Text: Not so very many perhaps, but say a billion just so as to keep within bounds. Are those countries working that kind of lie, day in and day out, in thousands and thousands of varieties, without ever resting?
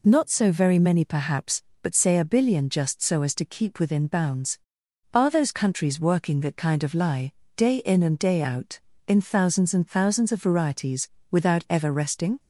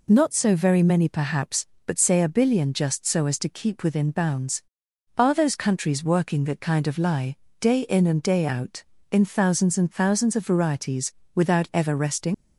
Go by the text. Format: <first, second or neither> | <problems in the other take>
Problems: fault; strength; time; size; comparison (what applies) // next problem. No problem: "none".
first | leaves "resting" unfinished; at 12.3 s; 85 ms